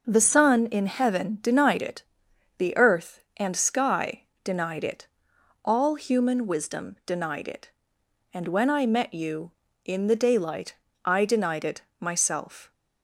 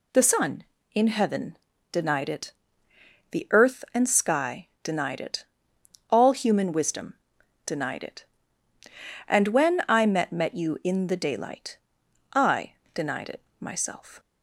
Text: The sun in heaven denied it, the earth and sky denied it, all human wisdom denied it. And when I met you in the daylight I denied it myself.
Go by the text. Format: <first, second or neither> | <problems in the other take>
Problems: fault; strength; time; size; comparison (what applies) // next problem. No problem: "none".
first | pauses between "heaven" and "denied"; slight; at 1.5 s; 0.36 s long // pauses between "sky" and "denied"; slight; at 4.6 s; 0.16 s long; slight in the first // pauses between "wisdom" and "denied"; noticeable; at 7.1 s; 0.50 s long // says "met" twice; at 10.3 s // pauses between "daylight" and "I"; noticeable; at 11.7 s; 0.56 s long; slight in the first // pauses between "I" and "denied"; slight; at 12.7 s; 0.22 s long // pauses between "it" and "myself"; slight; at 13.4 s; 0.18 s long; slight in the first